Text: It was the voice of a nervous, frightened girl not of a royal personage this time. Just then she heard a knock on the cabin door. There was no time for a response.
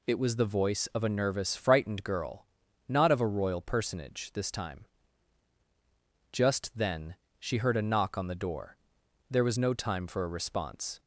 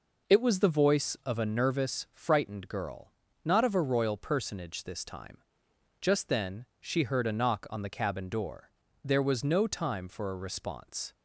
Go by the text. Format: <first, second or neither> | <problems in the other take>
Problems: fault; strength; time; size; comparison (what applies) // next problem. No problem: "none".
second | pauses between "girl" and "not"; at 2.4 s; 0.44 s long; slight in the second // pauses between "then" and "she"; slight; at 7.1 s; 0.24 s long; slight in the second // skips "cabin"; at 8.3 s